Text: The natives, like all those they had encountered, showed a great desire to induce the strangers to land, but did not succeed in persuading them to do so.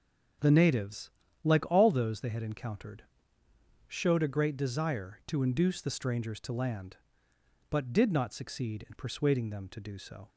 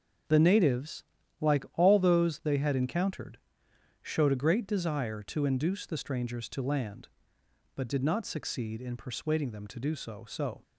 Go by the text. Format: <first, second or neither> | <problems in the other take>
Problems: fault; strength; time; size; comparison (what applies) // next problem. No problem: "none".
first | starts louder than the rest; until 1.6 s; 6.5 dB; also in the first // says "so" twice; at 10.2 s